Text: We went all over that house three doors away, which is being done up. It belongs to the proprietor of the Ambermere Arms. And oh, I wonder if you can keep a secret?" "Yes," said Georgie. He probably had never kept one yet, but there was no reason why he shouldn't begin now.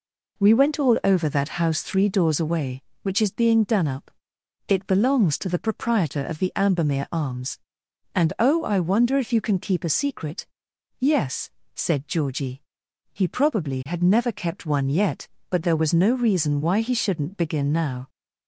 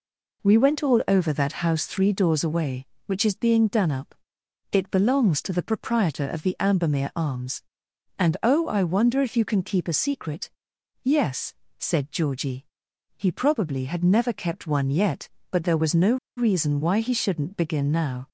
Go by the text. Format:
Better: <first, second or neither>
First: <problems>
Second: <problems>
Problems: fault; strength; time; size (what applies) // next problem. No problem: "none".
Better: first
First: none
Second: pauses between "no" and "reason"; slight; at 16.1 s; 0.21 s long